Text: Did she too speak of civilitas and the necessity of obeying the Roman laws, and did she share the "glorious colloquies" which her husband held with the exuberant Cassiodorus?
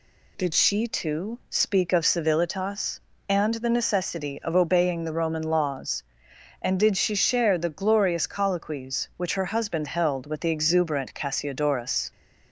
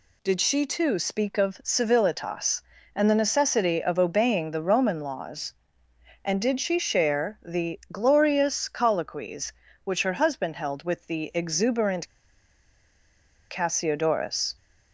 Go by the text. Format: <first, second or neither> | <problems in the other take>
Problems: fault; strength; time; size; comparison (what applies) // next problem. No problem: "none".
first | pauses between "exuberant" and "Cassiodorus"; strong; at 12.0 s; 1.4 s long